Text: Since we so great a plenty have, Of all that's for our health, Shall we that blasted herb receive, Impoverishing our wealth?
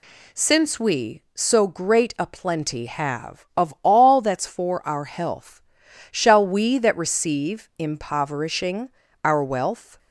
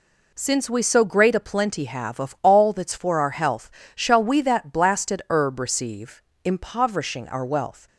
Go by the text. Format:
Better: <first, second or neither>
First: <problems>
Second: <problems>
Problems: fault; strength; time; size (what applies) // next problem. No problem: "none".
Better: second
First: skips "blasted herb"; at 6.9 s // pauses between "Impoverishing" and "our"; slight; at 8.8 s; 0.34 s long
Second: none